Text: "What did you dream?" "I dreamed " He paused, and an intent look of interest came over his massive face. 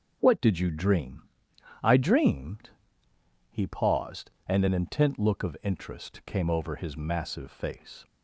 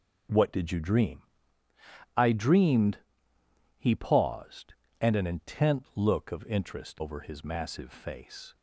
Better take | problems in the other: first | starts louder than the rest; until 2.2 s; 6.5 dB // skips "came"; at 7.0 s

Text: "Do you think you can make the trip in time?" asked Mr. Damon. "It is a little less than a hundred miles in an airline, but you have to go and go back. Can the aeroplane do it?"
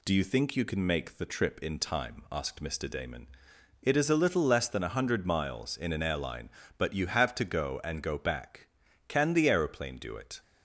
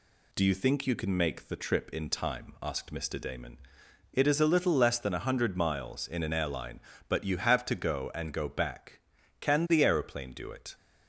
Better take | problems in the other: neither | none

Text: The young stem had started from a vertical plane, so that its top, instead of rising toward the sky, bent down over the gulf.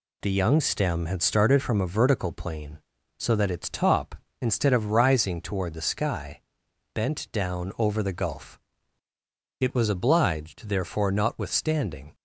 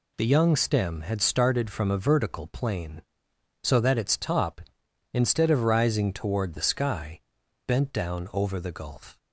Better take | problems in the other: second | goes on to say "It was obliged therefore notwithstanding"; strong; from 9.6 s on; 2.5 s long

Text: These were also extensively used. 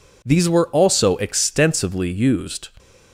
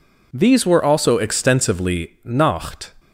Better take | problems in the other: first | says "nacht" for "used"; at 2.2 s

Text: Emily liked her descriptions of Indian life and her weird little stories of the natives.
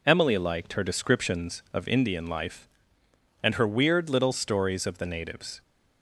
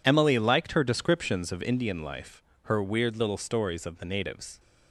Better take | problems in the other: first | skips "and"; at 2.5 s

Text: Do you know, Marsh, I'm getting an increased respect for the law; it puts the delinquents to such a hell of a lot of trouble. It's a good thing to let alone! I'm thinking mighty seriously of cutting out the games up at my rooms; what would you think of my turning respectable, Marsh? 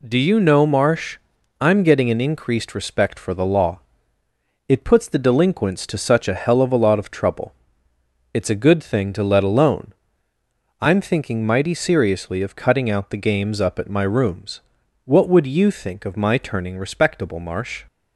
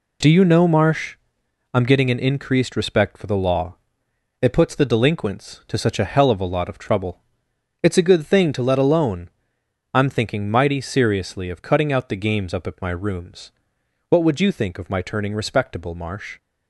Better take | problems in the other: neither | none

